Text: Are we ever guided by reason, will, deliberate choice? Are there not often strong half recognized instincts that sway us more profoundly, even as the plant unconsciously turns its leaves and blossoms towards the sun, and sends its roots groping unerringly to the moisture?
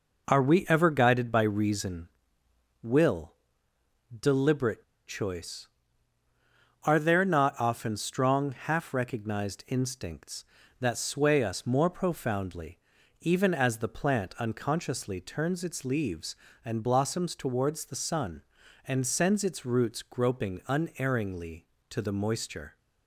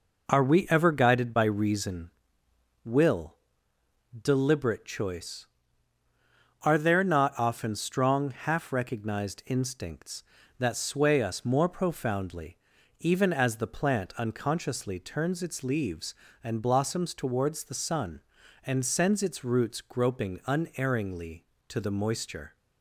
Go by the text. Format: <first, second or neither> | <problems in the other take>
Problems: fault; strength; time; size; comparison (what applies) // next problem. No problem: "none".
second | pauses between "deliberate" and "choice"; slight; at 4.8 s; 0.26 s long